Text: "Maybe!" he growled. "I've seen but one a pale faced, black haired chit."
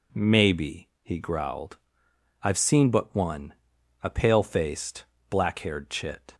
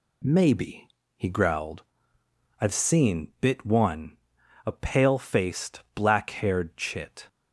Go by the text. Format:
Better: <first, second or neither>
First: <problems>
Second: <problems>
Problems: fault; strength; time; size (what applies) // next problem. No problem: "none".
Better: first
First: pauses between "one" and "a"; noticeable; at 3.5 s; 0.48 s long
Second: says "bit" for "but"; at 3.3 s // pauses between "one" and "a"; noticeable; at 4.1 s; 0.50 s long